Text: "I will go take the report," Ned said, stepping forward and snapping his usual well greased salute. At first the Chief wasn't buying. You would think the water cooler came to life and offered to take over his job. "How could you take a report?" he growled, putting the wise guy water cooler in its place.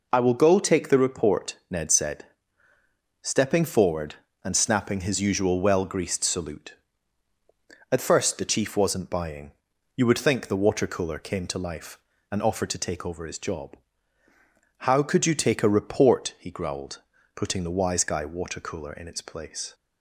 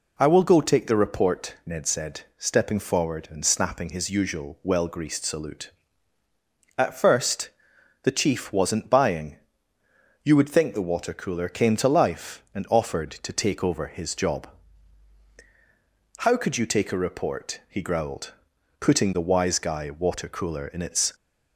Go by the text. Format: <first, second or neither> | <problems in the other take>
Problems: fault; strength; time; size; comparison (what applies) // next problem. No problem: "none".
first | pauses between "first" and "the"; noticeable; at 7.5 s; 0.52 s long // stops before "place"; at 21.1 s